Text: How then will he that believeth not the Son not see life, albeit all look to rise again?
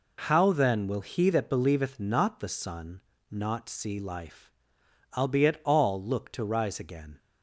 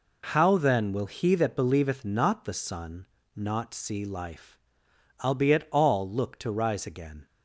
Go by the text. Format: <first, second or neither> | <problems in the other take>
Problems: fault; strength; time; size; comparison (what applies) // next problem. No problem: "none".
neither | pauses between "Son" and "not"; slight; the same in both